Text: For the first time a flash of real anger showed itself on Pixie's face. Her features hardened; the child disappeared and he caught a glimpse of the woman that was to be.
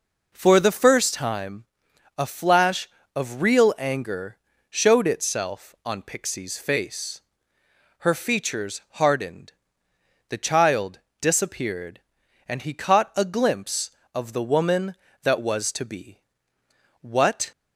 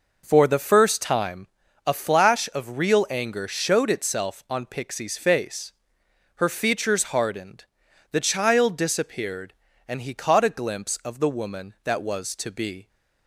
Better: second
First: pauses between "time" and "a"; noticeable; at 1.6 s; 0.54 s long // pauses between "anger" and "showed"; slight; at 4.3 s; 0.32 s long // pauses between "child" and "disappeared"; slight; at 11.0 s; 0.20 s long // goes on to say "What"; from 17.0 s on; 0.50 s long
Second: pauses between "time" and "a"; at 1.4 s; 0.38 s long

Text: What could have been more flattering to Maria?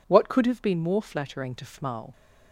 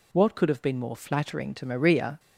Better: second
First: says "Fmal" for "Maria"; at 1.6 s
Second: none

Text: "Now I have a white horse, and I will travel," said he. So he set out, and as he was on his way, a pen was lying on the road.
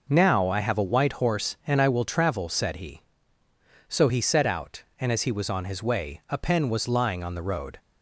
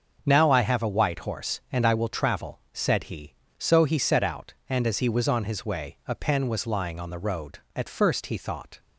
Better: first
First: none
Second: starts louder than the rest; until 1.2 s; 7 dB // goes on to say "At first he thought"; noticeable; from 7.7 s on; 1.0 s long

